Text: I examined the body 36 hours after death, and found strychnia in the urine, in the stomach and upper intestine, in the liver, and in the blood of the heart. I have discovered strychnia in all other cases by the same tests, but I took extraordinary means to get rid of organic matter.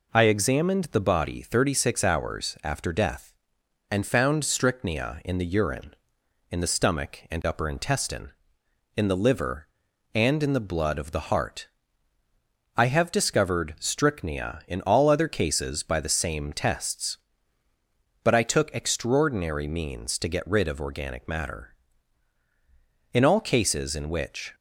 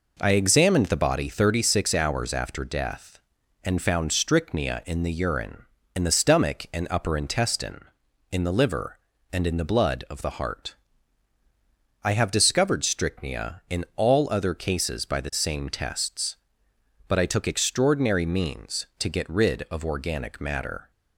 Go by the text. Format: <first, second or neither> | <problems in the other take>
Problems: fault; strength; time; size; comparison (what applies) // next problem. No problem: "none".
second | goes on to say "In all cases in which"; from 23.1 s on; 1.4 s long